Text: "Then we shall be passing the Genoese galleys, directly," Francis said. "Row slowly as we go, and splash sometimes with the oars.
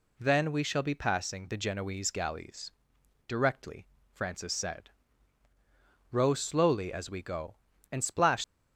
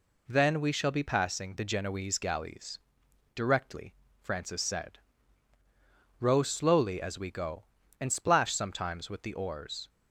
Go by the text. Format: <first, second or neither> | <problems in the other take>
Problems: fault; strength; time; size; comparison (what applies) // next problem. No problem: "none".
second | stops before "sometimes with the oars"; at 8.4 s